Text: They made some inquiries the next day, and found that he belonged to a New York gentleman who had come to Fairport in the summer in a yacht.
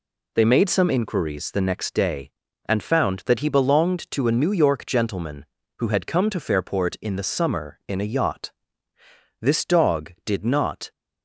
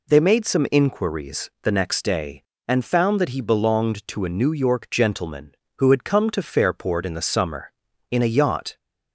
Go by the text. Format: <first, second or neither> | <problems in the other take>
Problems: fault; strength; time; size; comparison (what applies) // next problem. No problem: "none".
second | goes on to say "This dog did not"; from 9.4 s on; 1.5 s long